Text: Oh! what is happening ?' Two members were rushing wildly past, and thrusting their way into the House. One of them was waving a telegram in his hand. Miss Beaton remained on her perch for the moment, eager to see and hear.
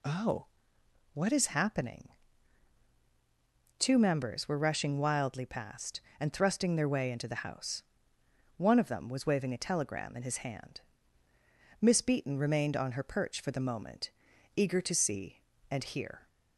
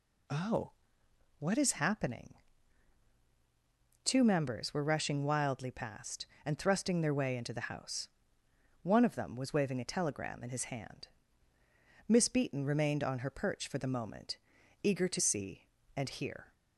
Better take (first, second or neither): neither